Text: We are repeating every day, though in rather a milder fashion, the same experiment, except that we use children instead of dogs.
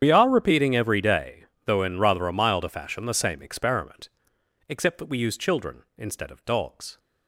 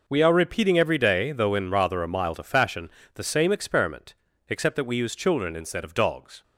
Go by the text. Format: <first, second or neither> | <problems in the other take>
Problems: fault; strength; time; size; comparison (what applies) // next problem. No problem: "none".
second | loses the start of "We"; at 0.0 s; 65 ms // starts louder than the rest; strong; until 1.0 s; 9 dB